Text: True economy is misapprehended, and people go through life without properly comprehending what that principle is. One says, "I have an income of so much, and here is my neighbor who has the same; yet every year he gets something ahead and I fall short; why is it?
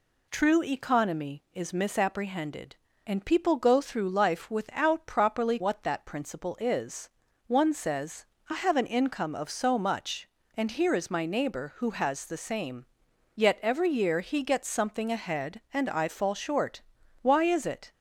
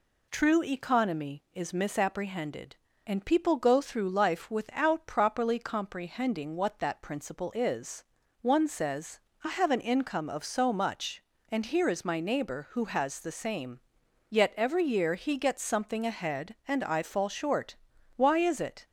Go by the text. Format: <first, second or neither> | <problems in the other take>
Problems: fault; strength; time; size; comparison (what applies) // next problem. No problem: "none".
second | skips "comprehending"; at 5.5 s